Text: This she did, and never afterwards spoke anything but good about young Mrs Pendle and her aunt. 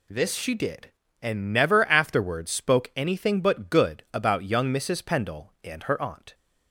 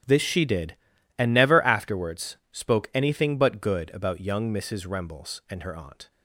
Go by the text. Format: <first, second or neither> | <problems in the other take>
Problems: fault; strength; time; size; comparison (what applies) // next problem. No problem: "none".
first | starts louder than the rest; strong; until 1.4 s; 10 dB // pauses between "afterwards" and "spoke"; slight; at 2.3 s; 0.16 s long // says "Rembles" for "Pendle"; at 4.8 s